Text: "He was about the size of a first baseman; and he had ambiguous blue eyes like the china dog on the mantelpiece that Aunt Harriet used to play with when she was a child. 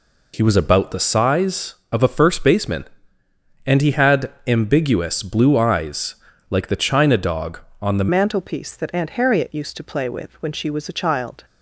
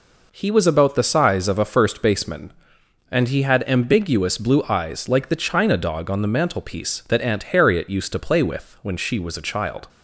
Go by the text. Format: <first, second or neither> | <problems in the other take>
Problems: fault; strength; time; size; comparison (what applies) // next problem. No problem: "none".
second | pauses between "had" and "ambiguous"; slight; at 4.3 s; 0.16 s long // pauses between "eyes" and "like"; slight; at 6.1 s; 0.34 s long // changes voice at "mantelpiece"; from 8.1 s on; 3.3 s long